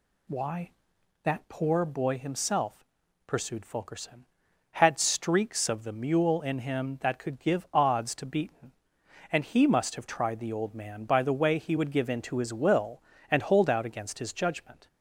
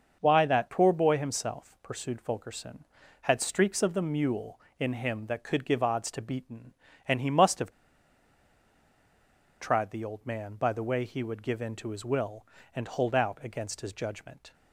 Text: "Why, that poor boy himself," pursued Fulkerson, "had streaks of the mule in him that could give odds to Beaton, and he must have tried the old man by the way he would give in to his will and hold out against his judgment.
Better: first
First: none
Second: starts louder than the rest; until 1.2 s; 6.5 dB // pauses between "have" and "tried"; strong; at 7.7 s; 1.9 s long

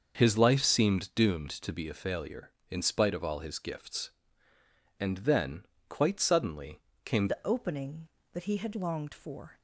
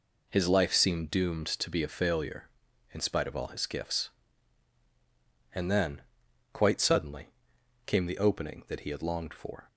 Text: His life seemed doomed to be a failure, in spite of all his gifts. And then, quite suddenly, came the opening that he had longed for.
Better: second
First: starts louder than the rest; until 1.1 s; 6.5 dB // changes voice at "the"; from 7.2 s on; 2.4 s long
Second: none

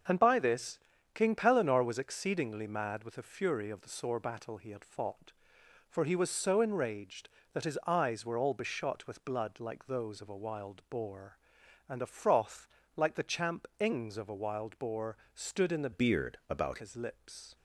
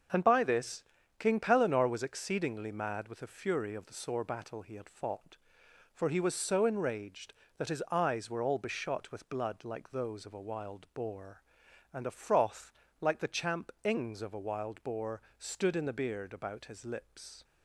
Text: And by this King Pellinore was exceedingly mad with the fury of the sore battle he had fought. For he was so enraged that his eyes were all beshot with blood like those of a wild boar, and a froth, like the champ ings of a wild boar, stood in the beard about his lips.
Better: second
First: starts louder than the rest; until 1.4 s; 6.5 dB // pauses between "this" and "King"; slight; at 0.7 s; 0.36 s long // changes voice from "beard" to "about"; from 15.9 to 16.7 s; 0.8 s long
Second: starts louder than the rest; until 1.4 s; 6.5 dB // pauses between "this" and "King"; slight; at 0.8 s; 0.36 s long

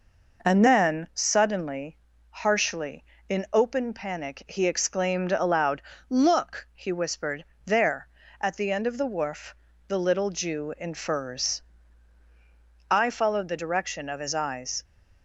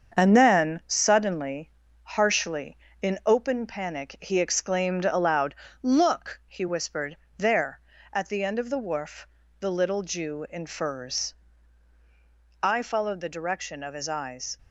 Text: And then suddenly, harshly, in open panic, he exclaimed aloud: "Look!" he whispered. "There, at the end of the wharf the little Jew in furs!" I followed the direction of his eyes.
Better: first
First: pauses between "wharf" and "the"; slight; at 9.5 s; 0.34 s long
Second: gets quieter; noticeable; throughout; 4.5 dB // pauses between "wharf" and "the"; slight; at 9.2 s; 0.34 s long

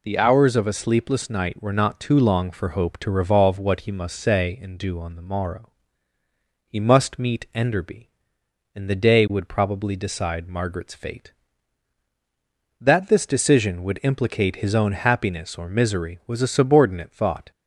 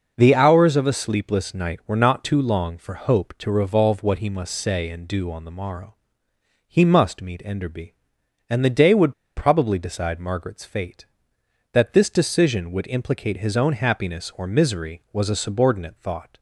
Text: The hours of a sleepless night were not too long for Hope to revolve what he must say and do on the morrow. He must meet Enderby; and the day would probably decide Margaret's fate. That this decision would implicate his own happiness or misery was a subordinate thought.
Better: first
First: none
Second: pauses between "would" and "probably"; slight; at 9.1 s; 0.24 s long

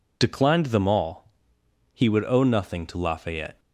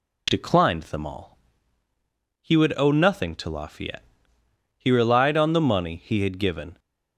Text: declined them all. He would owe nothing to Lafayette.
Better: first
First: none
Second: goes on to say "He relied on the money he had given"; strong; from 4.7 s on; 2.0 s long

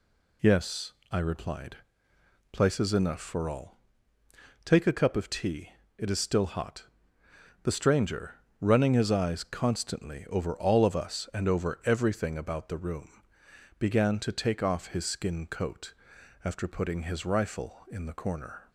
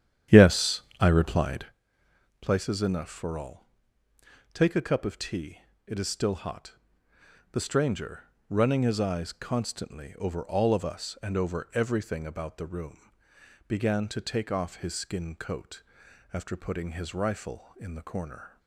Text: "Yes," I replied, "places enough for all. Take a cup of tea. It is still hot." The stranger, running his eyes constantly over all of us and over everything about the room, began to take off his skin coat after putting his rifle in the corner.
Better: first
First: pauses between "coat" and "after"; noticeable; at 15.9 s; 0.50 s long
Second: starts louder than the rest; strong; until 1.7 s; 10 dB // pauses between "coat" and "after"; noticeable; at 15.8 s; 0.50 s long

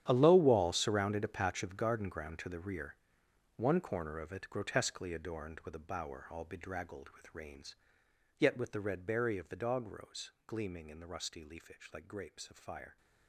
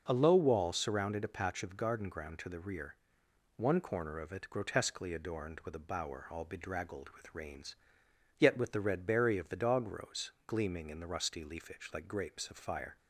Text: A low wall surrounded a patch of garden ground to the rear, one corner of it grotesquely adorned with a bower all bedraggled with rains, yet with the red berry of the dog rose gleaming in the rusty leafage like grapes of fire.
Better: second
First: gets quieter; strong; throughout; 15.5 dB // pauses between "rose" and "gleaming"; slight; at 10.3 s; 0.16 s long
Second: pauses between "rose" and "gleaming"; slight; at 10.3 s; 0.16 s long

